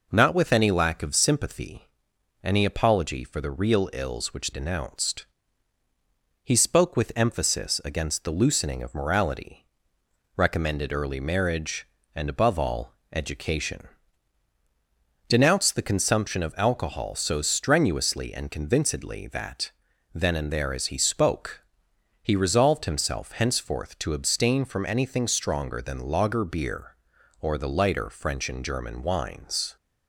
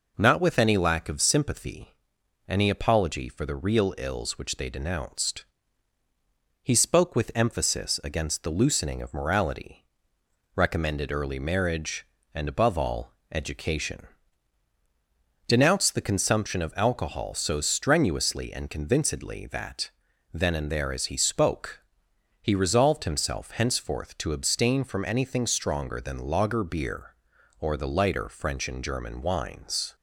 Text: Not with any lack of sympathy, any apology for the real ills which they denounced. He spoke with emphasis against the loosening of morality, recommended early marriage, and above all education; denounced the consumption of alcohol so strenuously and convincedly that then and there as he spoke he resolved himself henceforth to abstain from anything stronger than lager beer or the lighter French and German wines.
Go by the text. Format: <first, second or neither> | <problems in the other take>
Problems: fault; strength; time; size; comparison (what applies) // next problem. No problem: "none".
second | skips "they"; at 4.5 s // pauses between "all" and "education"; slight; at 12.9 s; 0.18 s long; slight in the second // pauses between "that" and "then"; at 19.6 s; 0.42 s long; also in the second // pauses between "spoke" and "he"; noticeable; at 21.6 s; 0.60 s long; noticeable in the second